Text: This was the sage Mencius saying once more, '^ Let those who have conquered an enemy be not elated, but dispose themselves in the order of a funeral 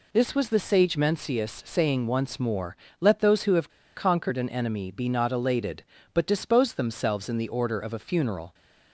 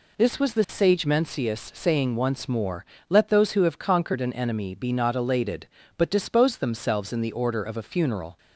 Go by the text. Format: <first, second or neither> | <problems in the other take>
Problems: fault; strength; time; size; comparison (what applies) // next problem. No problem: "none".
second | pauses between "have" and "conquered"; slight; at 3.6 s; 0.27 s long